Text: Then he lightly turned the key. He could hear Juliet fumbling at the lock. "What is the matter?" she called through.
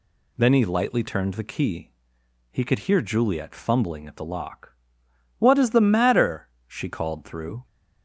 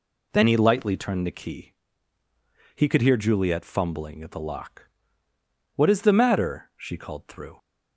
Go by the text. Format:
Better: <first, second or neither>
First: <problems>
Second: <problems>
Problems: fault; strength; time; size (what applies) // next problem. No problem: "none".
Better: neither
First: none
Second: none